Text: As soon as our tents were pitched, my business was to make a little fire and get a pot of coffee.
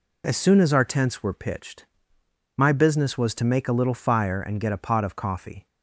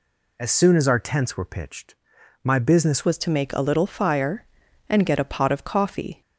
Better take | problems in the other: first | changes voice at "was"; from 3.0 s on; 3.2 s long

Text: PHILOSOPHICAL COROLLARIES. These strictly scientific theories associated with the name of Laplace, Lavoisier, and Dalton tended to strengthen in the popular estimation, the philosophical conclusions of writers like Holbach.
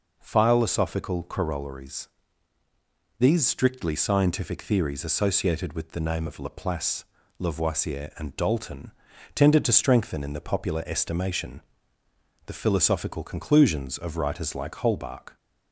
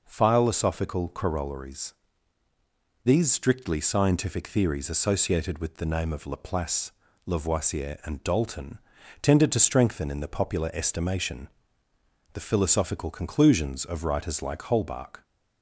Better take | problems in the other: neither | pauses between "Dalton" and "tended"; the same in both

